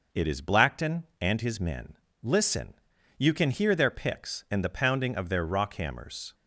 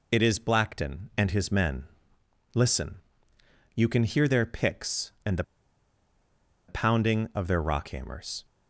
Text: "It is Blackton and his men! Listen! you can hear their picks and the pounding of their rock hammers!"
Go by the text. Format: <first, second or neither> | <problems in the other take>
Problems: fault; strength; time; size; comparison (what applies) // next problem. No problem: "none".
first | pauses between "the" and "pounding"; at 5.4 s; 1.2 s long